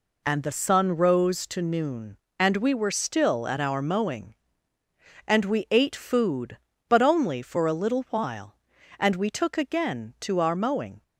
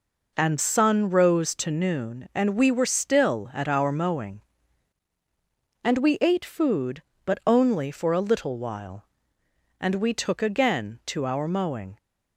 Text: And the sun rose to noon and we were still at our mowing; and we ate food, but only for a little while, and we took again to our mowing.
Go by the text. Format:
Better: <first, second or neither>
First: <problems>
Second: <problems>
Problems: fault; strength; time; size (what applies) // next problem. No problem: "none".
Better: first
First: none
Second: skips "the"; at 0.5 s